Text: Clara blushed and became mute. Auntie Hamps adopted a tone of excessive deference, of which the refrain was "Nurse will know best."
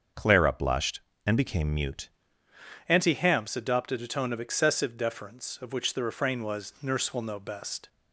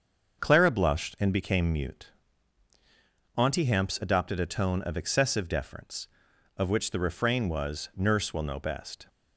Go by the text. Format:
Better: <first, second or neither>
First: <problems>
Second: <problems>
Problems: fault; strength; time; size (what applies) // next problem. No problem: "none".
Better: second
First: starts louder than the rest; until 1.3 s; 6.5 dB // changes voice at "Auntie"; from 2.8 s on; 5.0 s long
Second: starts louder than the rest; until 1.4 s; 6.5 dB